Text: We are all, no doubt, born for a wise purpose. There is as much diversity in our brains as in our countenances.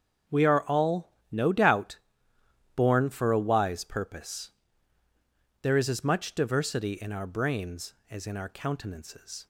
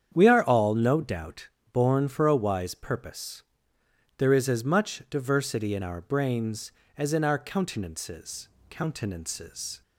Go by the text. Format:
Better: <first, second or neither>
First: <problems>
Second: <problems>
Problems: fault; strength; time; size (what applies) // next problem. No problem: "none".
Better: first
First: starts louder than the rest; until 1.4 s; 7 dB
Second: starts louder than the rest; strong; until 1.1 s; 8.5 dB // says "countenances" twice; at 8.6 s